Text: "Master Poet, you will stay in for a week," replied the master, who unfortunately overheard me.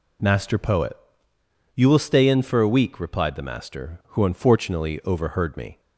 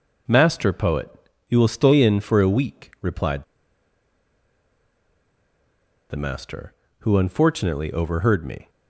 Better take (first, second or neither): first